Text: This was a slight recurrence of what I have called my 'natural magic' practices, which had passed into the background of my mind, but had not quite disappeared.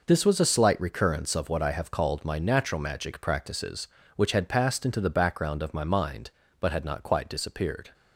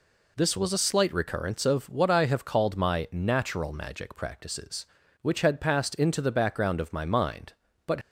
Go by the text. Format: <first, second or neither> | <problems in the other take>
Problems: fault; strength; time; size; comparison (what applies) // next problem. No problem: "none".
first | stops before "had not quite disappeared"; at 8.0 s